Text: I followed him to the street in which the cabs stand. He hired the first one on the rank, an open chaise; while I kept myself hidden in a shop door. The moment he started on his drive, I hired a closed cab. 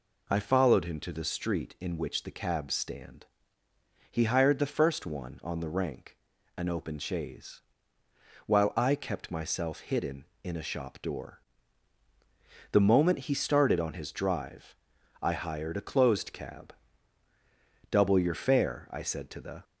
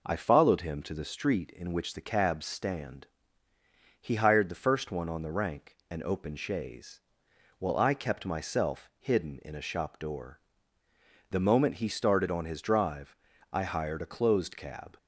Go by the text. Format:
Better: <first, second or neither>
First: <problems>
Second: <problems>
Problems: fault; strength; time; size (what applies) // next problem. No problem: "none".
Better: second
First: goes on to say "Double your fare I said to the"; strong; from 17.8 s on; 1.7 s long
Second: none